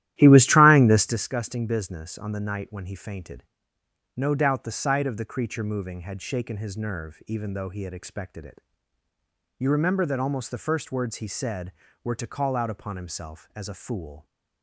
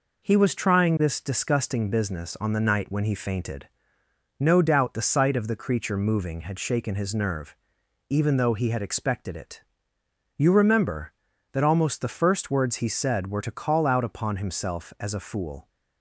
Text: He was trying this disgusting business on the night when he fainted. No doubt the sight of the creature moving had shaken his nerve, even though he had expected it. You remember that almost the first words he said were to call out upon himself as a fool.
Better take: second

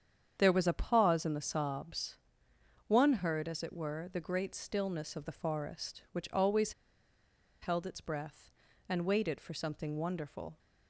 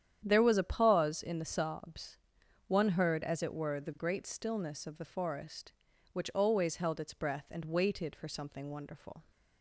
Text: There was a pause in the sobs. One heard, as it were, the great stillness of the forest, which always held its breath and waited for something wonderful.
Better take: second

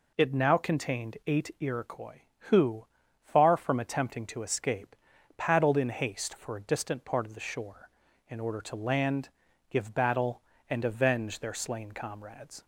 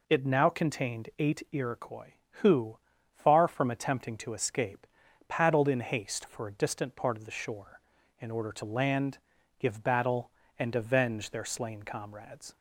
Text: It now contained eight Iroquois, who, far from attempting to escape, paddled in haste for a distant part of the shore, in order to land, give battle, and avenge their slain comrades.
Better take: neither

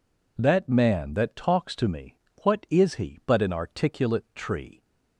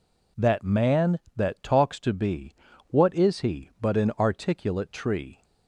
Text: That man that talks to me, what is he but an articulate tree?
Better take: first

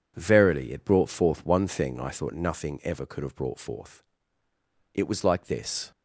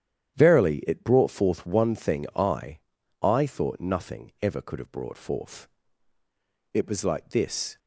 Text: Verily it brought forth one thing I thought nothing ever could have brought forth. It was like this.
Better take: first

